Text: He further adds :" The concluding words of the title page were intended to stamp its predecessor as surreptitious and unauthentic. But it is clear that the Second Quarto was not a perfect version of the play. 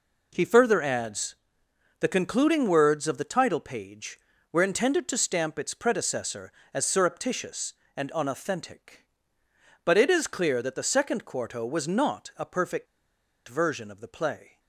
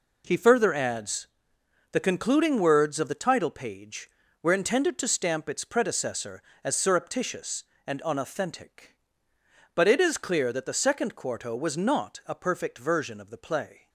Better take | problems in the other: second | pauses between "perfect" and "version"; noticeable; at 12.8 s; 0.61 s long

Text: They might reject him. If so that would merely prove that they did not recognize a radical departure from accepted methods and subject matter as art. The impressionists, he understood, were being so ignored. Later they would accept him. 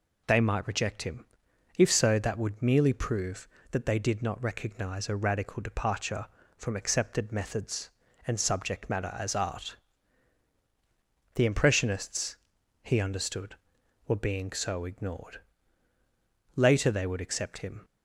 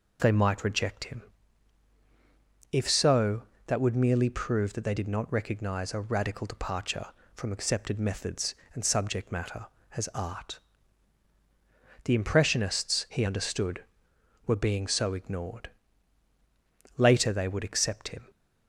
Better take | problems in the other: neither | none

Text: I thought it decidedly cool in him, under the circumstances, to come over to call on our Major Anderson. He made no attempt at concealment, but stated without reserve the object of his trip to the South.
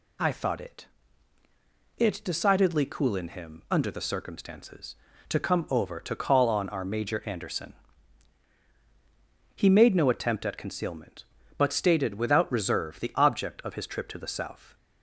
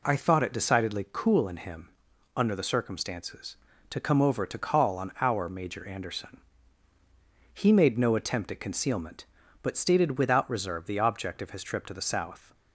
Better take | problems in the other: second | says "it" twice; at 1.9 s

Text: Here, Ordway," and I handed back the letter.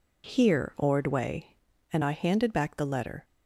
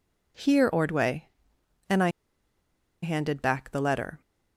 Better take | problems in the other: first | pauses between "I" and "handed"; noticeable; at 2.0 s; 0.92 s long

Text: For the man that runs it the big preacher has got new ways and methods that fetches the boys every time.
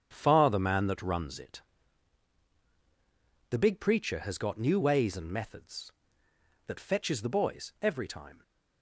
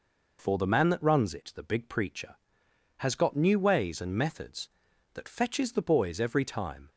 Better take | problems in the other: second | starts louder than the rest; strong; until 1.1 s; 9 dB // says "Far" for "For"; at 0.1 s // pauses between "it" and "the"; strong; at 1.6 s; 1.8 s long

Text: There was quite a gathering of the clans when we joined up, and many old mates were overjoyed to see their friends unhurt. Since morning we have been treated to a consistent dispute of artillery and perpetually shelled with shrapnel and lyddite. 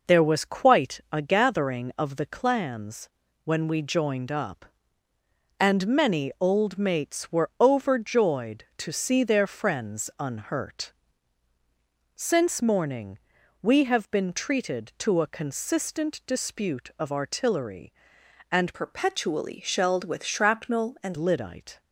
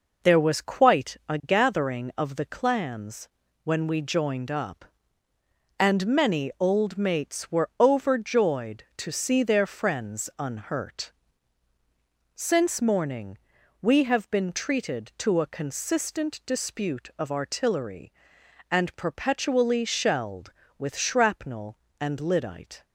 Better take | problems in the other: second | pauses between "clans" and "when"; slight; at 3.0 s; 0.36 s long; slight in the second // pauses between "morning" and "we"; at 13.1 s; 0.44 s long; also in the second // changes voice from "perpetually" to "and"; from 18.7 to 21.1 s; 2.4 s long

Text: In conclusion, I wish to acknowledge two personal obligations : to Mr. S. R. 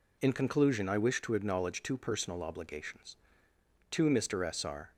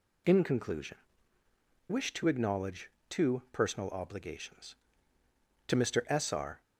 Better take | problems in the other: first | skips "I"; at 1.4 s // pauses between "acknowledge" and "two"; slight; at 2.8 s; 0.20 s long

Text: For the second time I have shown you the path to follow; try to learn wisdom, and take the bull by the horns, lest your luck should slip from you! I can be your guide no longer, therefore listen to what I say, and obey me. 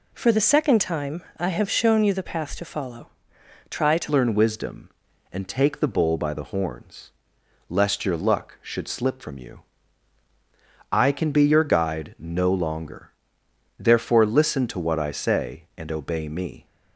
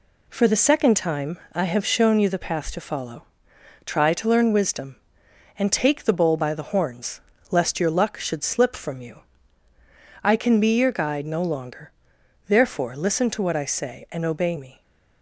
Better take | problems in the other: second | changes voice at "learn"; from 4.0 s on; 12.6 s long

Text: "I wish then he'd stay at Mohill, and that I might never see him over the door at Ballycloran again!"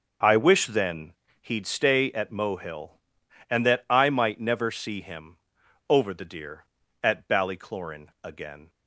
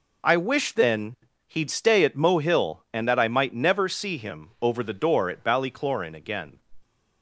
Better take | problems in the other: second | pauses between "then" and "he'd"; slight; at 1.1 s; 0.28 s long; slight in the second // pauses between "him" and "over"; noticeable; at 5.3 s; 0.52 s long // says "deer" for "door"; at 6.2 s

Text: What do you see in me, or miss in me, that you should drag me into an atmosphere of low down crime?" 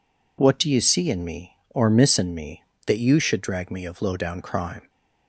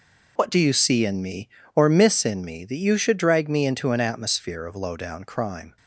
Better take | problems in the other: second | skips "into an atmosphere"; at 3.8 s

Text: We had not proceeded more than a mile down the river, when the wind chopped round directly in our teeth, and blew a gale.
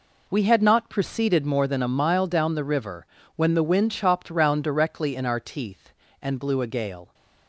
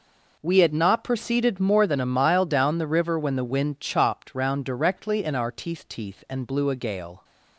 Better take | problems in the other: first | says "teeth" twice; at 5.8 s

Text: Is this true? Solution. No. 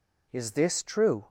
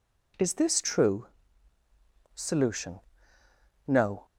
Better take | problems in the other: second | stops before "Solution No"; at 1.2 s

